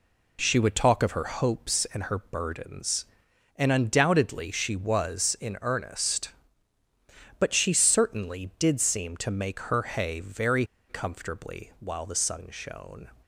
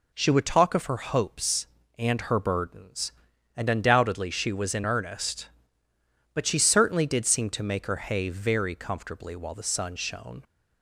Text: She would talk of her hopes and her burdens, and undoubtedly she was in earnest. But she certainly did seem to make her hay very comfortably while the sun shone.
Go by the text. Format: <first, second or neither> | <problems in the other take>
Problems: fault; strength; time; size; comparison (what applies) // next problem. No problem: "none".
second | pauses between "very" and "comfortably"; slight; at 10.6 s; 0.25 s long